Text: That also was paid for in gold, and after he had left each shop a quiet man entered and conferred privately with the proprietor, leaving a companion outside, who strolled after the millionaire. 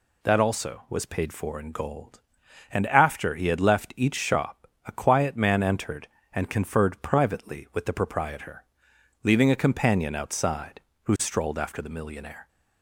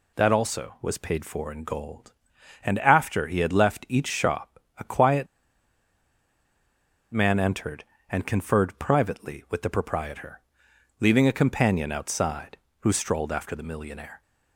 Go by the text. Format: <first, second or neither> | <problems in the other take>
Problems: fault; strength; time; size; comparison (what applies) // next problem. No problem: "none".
first | pauses between "shop" and "a"; slight; at 4.5 s; 0.18 s long; slight in the first // pauses between "quiet" and "man"; strong; at 5.2 s; 1.8 s long